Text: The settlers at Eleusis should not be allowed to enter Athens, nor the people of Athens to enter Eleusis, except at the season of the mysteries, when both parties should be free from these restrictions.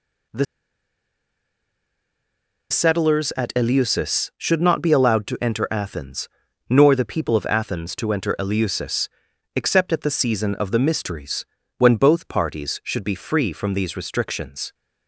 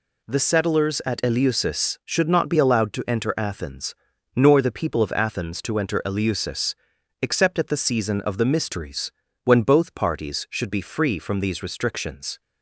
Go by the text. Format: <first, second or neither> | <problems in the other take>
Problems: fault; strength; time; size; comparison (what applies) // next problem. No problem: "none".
second | pauses between "The" and "settlers"; strong; at 0.4 s; 2.2 s long